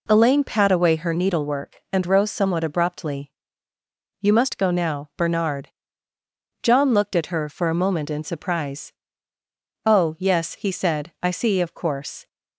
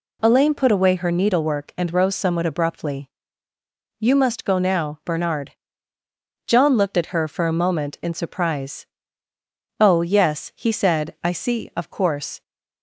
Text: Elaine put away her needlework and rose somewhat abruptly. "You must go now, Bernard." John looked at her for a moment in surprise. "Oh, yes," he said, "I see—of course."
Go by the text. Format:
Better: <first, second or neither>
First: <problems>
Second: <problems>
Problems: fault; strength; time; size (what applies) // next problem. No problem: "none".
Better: second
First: says "pat" for "put"; at 0.4 s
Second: none